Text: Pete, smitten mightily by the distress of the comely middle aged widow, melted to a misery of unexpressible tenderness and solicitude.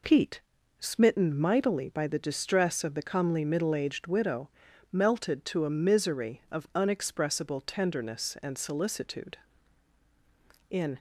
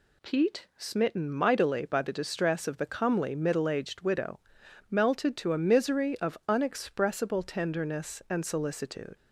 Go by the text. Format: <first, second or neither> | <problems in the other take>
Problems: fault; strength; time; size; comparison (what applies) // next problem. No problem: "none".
second | goes on to say "In"; slight; from 10.7 s on; 0.28 s long